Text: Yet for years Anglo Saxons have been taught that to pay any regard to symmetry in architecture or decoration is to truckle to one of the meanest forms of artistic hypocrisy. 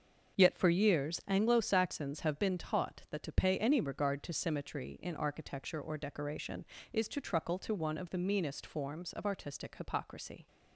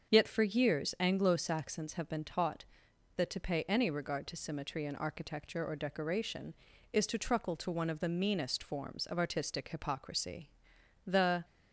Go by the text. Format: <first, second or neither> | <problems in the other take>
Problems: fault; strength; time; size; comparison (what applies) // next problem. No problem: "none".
first | starts louder than the rest; until 1.1 s; 7 dB; also in the first // goes on to say "The"; slight; from 11.0 s on; 0.38 s long